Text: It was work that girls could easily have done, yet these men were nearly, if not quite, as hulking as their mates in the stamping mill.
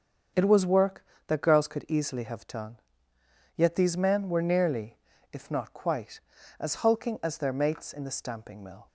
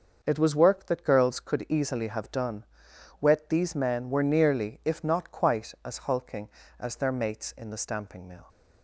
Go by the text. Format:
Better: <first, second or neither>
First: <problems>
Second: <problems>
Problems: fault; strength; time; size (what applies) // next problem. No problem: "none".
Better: first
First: starts louder than the rest; strong; until 1.5 s; 7 dB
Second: starts louder than the rest; noticeable; until 1.2 s; 6 dB // says "wet" for "yet"; at 3.1 s